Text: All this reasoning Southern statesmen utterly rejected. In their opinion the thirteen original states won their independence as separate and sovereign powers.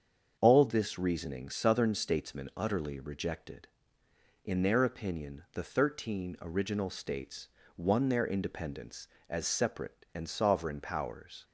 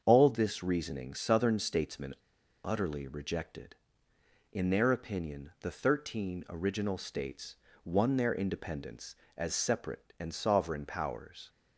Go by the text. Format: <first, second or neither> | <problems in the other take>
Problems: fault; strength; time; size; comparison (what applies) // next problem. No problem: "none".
first | starts louder than the rest; until 1.0 s; 7 dB; also in the first // pauses between "statesmen" and "utterly"; noticeable; at 2.1 s; 0.48 s long // pauses between "states" and "won"; slight; at 7.5 s; 0.28 s long; slight in the first